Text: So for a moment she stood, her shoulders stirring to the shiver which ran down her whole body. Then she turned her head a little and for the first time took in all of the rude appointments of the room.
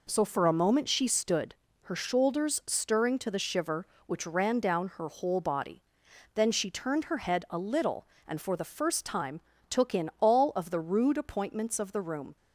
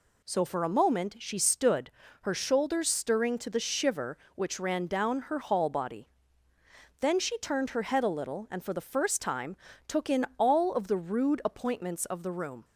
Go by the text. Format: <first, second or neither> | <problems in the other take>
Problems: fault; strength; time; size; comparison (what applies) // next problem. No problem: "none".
first | says "hall" for "whole"; at 5.3 s // pauses between "time" and "took"; slight; at 9.5 s; 0.32 s long; slight in the first